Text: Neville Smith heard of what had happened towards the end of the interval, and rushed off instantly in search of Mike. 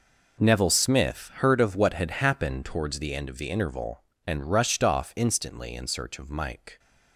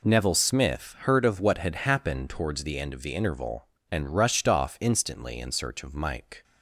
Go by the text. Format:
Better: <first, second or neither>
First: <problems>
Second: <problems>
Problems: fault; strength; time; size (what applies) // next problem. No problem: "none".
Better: second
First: gets quieter; strong; throughout; 14 dB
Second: none